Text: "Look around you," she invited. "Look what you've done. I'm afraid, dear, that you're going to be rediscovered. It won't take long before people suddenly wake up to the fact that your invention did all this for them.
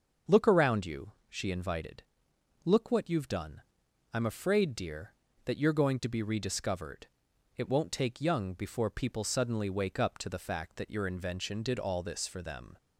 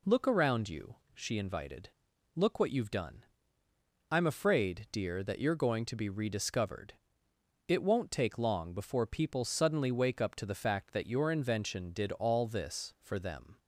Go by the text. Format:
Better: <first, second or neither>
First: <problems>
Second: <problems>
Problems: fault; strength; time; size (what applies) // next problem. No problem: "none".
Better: second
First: starts louder than the rest; until 1.4 s; 6.5 dB // says "young" for "long"; at 8.2 s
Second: none